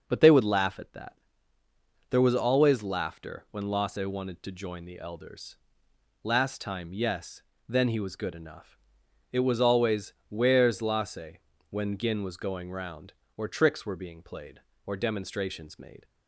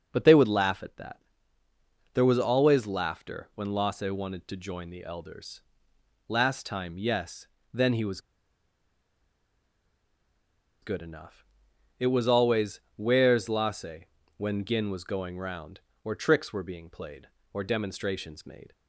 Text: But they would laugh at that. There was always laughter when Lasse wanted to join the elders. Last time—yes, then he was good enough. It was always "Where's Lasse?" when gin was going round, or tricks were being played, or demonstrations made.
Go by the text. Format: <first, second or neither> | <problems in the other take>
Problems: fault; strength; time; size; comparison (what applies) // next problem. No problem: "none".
first | pauses between "was" and "good"; strong; at 8.1 s; 2.6 s long // pauses between "always" and "Where's"; slight; at 12.7 s; 0.16 s long; slight in the first